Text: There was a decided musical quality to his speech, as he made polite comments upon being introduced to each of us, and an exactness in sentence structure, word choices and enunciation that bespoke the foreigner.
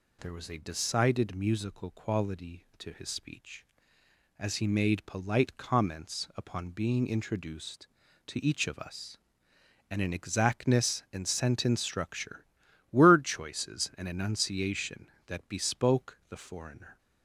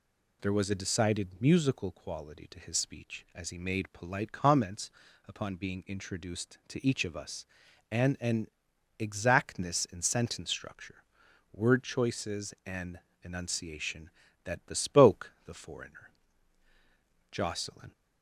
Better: first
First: none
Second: pauses between "comments" and "upon"; at 4.8 s; 0.38 s long // pauses between "an" and "exactness"; noticeable; at 8.4 s; 0.50 s long // pauses between "and" and "enunciation"; slight; at 12.9 s; 0.22 s long // goes on to say "Jocelyn"; from 17.3 s on; 0.60 s long

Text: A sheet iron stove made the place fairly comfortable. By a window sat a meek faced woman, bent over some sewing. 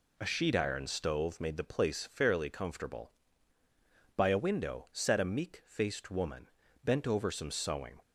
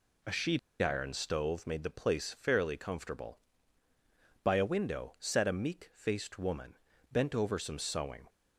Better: first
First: none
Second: pauses between "sheet" and "iron"; slight; at 0.5 s; 0.23 s long

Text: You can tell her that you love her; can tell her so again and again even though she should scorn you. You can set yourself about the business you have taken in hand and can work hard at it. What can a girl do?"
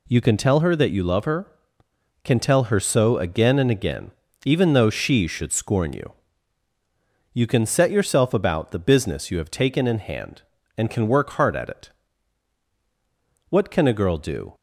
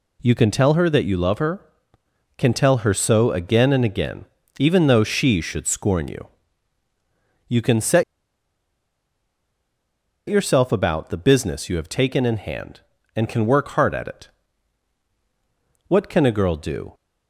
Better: first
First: pauses between "again" and "even"; slight; at 4.1 s; 0.34 s long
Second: pauses between "again" and "even"; slight; at 4.2 s; 0.34 s long // pauses between "set" and "yourself"; strong; at 8.0 s; 2.2 s long

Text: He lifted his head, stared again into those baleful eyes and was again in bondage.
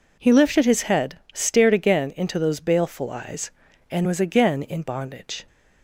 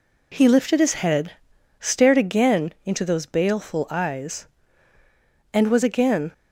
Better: first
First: none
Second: stops before "in bondage"; at 6.3 s

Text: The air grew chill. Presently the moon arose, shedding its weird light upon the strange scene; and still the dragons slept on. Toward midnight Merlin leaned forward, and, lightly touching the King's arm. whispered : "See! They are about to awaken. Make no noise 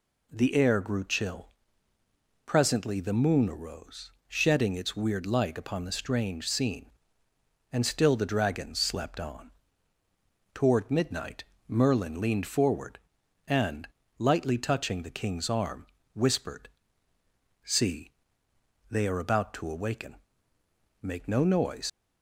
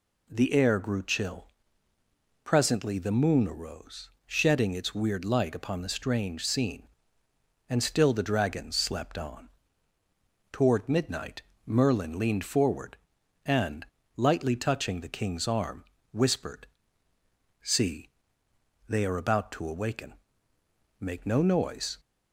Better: second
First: pauses between "midnight" and "Merlin"; slight; at 11.4 s; 0.24 s long // leaves "noise" unfinished; at 21.8 s; 120 ms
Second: pauses between "midnight" and "Merlin"; slight; at 11.4 s; 0.24 s long

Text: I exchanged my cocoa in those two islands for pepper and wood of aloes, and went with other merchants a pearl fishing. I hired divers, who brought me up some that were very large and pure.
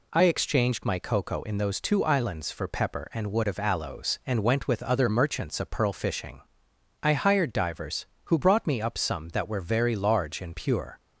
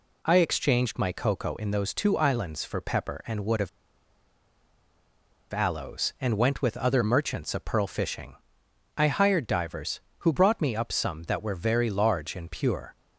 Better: first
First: none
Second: pauses between "of" and "aloes"; strong; at 3.6 s; 1.8 s long

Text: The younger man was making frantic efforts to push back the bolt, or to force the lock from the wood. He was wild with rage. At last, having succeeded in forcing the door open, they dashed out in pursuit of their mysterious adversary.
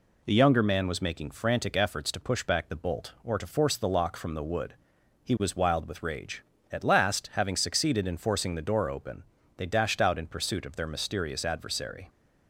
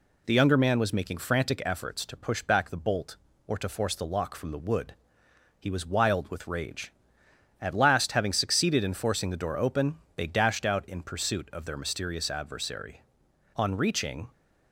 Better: first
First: none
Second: goes on to say "On reaching"; noticeable; from 13.5 s on; 0.72 s long

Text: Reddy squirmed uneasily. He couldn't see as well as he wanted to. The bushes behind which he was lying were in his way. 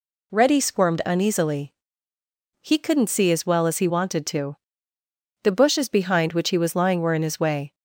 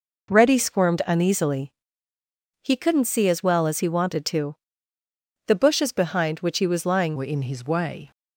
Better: first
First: none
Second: changes voice at "were"; from 7.1 s on; 1.0 s long

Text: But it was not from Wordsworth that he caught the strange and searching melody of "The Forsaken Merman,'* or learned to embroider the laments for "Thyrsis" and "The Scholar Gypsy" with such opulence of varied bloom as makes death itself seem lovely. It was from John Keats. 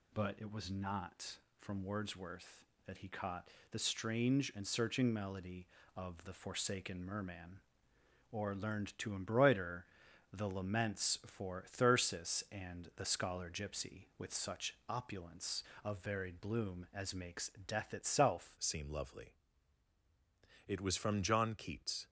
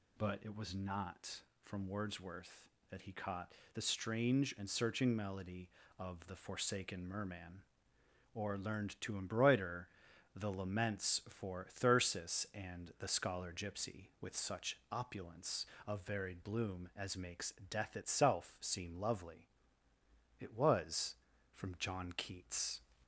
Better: second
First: pauses between "caught" and "the"; slight; at 3.4 s; 0.22 s long // pauses between "embroider" and "the"; at 9.8 s; 0.44 s long // pauses between "makes" and "death"; slight; at 17.4 s; 0.18 s long // changes voice at "seem"; from 18.5 s on; 3.5 s long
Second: pauses between "caught" and "the"; slight; at 3.5 s; 0.21 s long // pauses between "embroider" and "the"; at 9.8 s; 0.44 s long // pauses between "makes" and "death"; slight; at 17.5 s; 0.18 s long

